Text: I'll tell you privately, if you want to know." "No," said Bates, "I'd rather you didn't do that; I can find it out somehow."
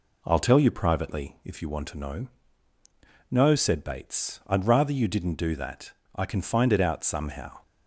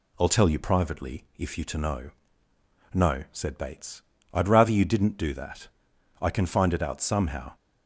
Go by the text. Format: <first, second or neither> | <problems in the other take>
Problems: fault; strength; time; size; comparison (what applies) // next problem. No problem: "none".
first | skips "want"; at 1.6 s